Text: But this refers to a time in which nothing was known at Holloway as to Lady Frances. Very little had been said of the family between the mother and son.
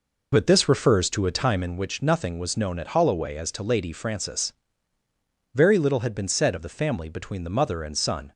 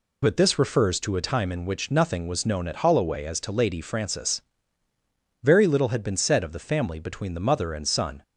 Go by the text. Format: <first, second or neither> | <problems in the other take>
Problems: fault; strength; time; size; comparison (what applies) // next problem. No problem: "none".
second | starts louder than the rest; noticeable; until 1.8 s; 4.5 dB